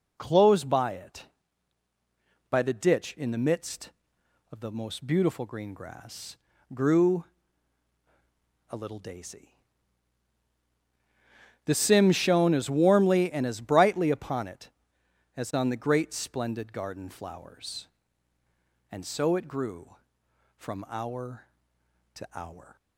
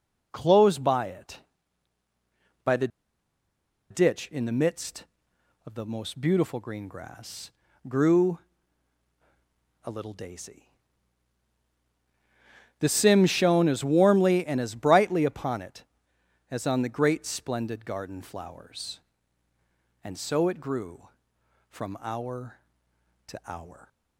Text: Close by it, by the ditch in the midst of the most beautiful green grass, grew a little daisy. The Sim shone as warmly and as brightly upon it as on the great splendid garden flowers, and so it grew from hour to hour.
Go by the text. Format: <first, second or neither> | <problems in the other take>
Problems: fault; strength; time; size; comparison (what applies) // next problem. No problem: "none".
first | pauses between "the" and "ditch"; at 2.8 s; 1.0 s long // pauses between "grew" and "a"; strong; at 8.3 s; 1.4 s long; strong in the first